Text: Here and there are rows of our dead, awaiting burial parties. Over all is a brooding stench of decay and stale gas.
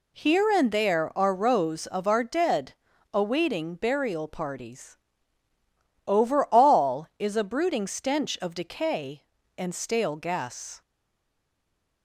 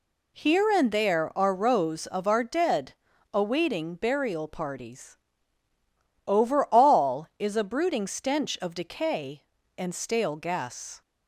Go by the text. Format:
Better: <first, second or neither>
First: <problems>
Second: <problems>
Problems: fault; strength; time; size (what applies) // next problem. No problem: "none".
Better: second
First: stays silent after the last word; noticeable; from 10.8 s on; 1.2 s long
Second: none